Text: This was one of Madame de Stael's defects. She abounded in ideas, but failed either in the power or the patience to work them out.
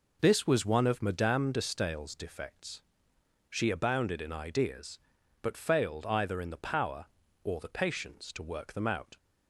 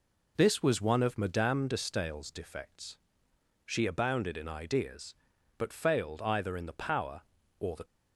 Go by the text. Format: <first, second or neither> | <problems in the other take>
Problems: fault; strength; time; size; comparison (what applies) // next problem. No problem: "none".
first | stops before "patience to work them out"; at 7.8 s